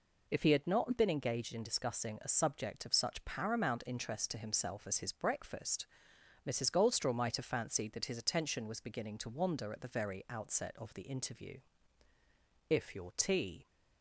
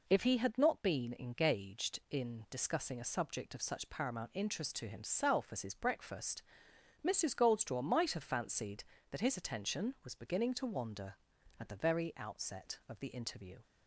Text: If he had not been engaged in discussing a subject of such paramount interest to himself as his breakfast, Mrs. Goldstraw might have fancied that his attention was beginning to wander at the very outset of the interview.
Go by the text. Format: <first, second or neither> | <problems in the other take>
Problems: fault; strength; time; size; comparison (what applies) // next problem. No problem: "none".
second | goes on to say "If your tea"; noticeable; from 12.6 s on; 0.98 s long